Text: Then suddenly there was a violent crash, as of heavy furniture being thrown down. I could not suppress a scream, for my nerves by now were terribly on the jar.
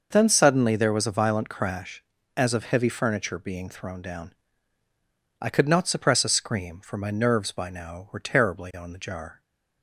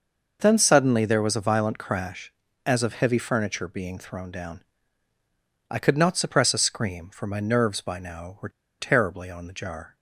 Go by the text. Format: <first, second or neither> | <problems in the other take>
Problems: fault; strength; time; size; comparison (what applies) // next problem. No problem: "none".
first | pauses between "were" and "terribly"; slight; at 8.4 s; 0.30 s long